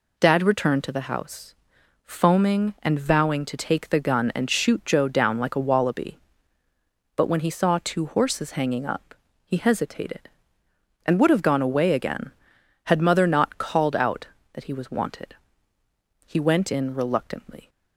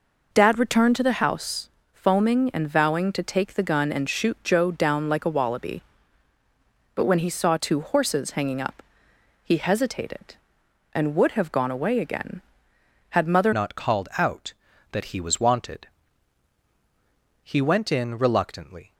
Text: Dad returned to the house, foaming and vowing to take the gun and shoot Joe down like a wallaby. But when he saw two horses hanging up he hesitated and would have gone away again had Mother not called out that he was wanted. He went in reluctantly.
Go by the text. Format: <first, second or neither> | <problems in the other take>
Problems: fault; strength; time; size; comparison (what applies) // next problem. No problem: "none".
first | pauses between "up" and "he"; noticeable; at 8.8 s; 0.62 s long; slight in the first // changes voice at "not"; from 13.5 s on; 5.4 s long